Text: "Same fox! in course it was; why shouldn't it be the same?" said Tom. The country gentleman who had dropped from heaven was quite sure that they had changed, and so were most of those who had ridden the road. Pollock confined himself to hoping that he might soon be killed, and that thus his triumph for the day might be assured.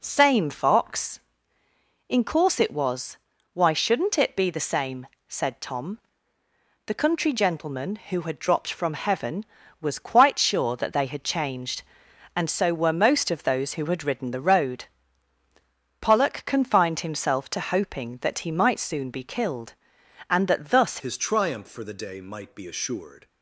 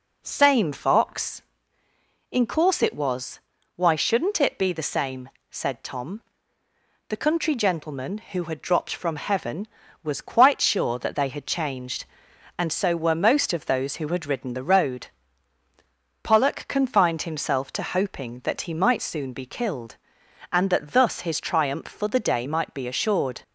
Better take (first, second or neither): second